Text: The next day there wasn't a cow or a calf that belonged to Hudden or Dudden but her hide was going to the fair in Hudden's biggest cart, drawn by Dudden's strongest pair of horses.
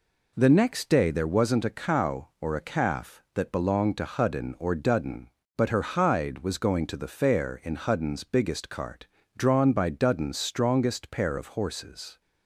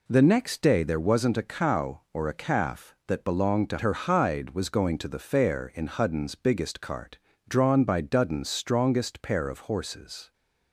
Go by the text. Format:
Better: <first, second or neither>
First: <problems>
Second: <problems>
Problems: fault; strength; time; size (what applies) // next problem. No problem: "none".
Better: first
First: none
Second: skips "Hudden or Dudden but"; at 3.7 s